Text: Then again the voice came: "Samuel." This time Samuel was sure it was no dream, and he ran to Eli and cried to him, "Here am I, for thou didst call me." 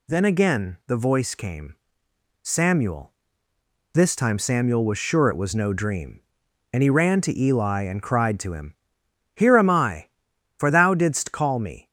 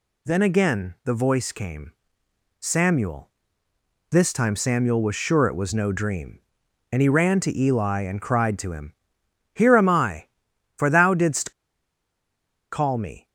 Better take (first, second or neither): first